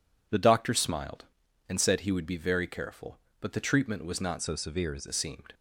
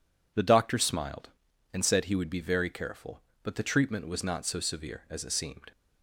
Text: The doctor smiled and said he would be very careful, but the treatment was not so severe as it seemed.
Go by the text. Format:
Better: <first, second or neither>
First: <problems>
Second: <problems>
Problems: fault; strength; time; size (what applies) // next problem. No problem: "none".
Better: second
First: changes voice from "so" to "as"; from 4.4 to 5.0 s; 0.6 s long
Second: none